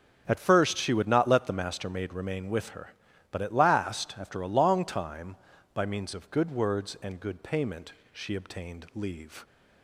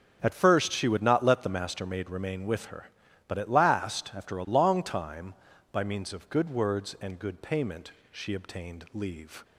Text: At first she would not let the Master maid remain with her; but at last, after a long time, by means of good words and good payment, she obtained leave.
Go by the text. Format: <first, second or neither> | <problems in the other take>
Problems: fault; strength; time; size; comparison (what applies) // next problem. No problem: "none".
neither | starts louder than the rest; the same in both